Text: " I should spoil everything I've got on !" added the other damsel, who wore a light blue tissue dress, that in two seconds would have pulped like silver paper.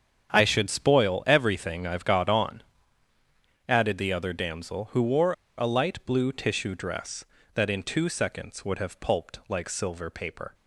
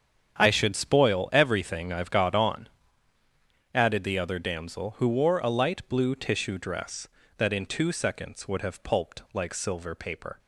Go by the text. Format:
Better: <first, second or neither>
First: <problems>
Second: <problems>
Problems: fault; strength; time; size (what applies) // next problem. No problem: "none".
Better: second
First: starts louder than the rest; strong; until 1.3 s; 7.5 dB // pauses between "wore" and "a"; slight; at 5.3 s; 0.24 s long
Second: starts louder than the rest; strong; until 1.3 s; 7.5 dB